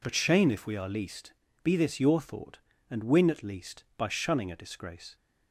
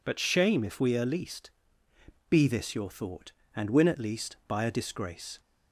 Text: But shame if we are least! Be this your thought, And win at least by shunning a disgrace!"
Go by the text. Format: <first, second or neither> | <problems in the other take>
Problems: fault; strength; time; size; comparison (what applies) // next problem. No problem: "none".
first | skips "shunning"; at 4.6 s